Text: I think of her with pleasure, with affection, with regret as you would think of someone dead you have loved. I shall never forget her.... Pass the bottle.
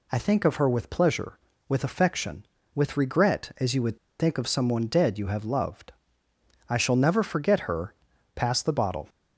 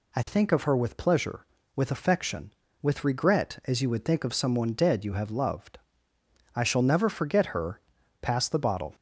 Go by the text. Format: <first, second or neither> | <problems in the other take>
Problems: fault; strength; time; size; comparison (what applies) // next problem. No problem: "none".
second | pauses between "would" and "think"; slight; at 3.9 s; 0.21 s long